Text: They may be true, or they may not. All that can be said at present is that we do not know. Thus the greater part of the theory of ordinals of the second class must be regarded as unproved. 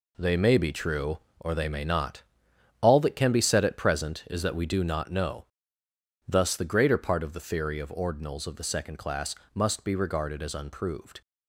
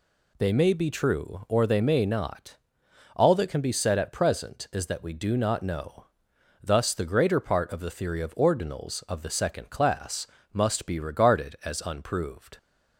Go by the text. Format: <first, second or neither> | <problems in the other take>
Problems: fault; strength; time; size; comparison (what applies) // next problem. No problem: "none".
second | gets quieter; strong; throughout; 8.5 dB // pauses between "class" and "must"; slight; at 9.3 s; 0.18 s long; slight in the second